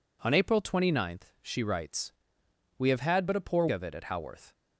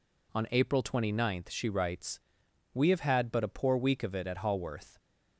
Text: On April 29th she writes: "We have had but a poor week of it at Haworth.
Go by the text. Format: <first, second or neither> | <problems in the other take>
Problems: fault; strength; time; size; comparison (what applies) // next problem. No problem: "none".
second | skips "week"; at 3.6 s